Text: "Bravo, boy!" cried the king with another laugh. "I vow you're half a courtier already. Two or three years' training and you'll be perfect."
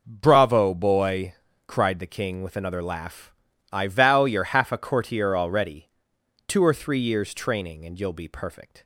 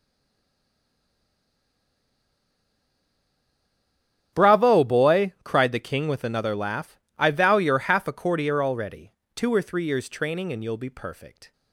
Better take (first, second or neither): first